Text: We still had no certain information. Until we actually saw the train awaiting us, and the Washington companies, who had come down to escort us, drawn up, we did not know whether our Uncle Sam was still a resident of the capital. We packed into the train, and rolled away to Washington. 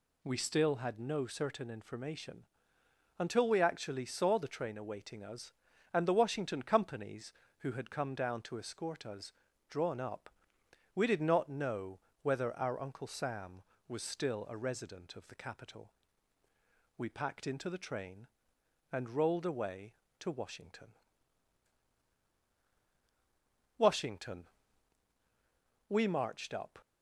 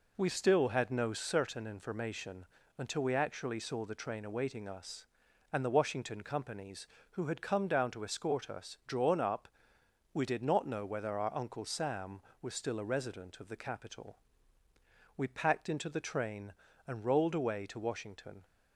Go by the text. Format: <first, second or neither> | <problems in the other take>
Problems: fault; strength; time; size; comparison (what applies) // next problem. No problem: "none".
second | pauses between "know" and "whether"; slight; at 11.9 s; 0.22 s long // goes on to say "WASHINGTON We marched up"; strong; from 23.7 s on; 3.0 s long